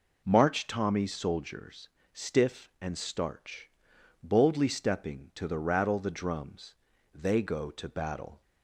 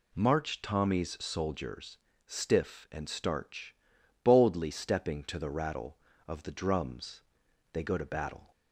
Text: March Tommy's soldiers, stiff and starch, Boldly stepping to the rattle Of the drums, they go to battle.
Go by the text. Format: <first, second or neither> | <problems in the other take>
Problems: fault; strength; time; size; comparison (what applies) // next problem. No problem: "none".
second | skips "Of"; at 5.9 s